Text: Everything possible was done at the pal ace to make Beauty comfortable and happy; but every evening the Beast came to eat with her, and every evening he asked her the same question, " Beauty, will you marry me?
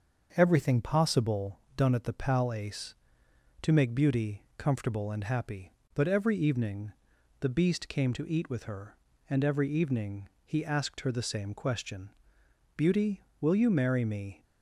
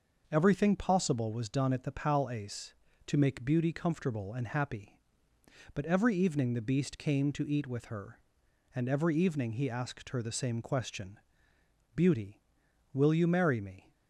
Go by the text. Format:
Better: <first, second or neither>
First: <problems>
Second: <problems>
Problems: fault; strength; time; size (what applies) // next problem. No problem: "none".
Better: second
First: starts louder than the rest; until 1.3 s; 7 dB // skips "was"; at 1.6 s // pauses between "evening" and "the"; noticeable; at 6.9 s; 0.48 s long // pauses between "evening" and "he"; slight; at 10.2 s; 0.18 s long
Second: starts louder than the rest; noticeable; until 1.3 s; 6 dB